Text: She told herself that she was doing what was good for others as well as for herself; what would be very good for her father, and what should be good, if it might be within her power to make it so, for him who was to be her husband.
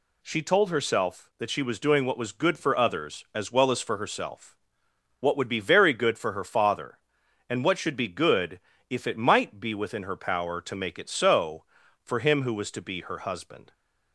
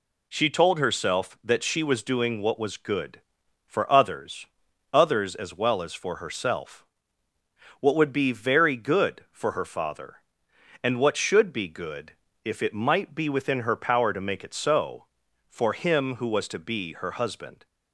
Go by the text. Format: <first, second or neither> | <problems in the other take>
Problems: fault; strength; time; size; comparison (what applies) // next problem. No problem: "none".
first | says "others" twice; at 4.9 s